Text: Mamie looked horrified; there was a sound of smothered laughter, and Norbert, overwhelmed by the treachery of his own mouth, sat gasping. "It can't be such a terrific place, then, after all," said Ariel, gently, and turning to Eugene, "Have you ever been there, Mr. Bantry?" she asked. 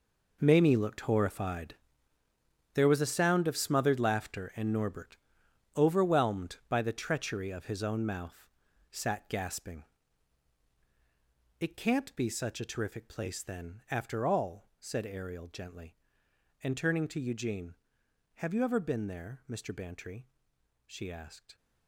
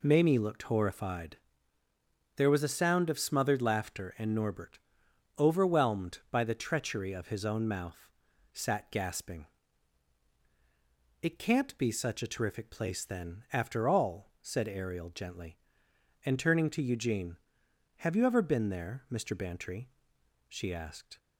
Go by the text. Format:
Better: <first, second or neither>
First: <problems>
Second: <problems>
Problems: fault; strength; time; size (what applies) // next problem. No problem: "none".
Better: second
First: gets quieter; strong; throughout; 14 dB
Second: none